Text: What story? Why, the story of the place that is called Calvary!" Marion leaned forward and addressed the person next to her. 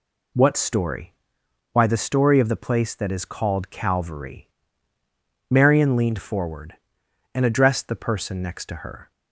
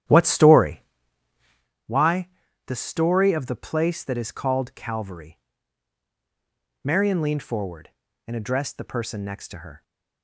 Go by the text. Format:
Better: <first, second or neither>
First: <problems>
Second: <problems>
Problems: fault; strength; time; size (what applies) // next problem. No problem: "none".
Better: first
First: none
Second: starts louder than the rest; strong; until 1.7 s; 11.5 dB